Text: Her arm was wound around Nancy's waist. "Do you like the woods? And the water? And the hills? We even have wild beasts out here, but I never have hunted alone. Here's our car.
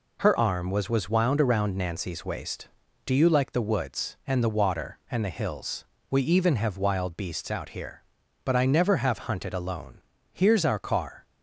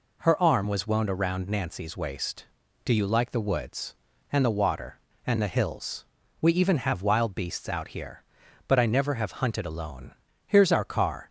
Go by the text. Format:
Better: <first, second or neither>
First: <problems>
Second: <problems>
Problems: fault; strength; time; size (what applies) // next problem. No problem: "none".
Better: second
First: says "was" twice; at 0.8 s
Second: none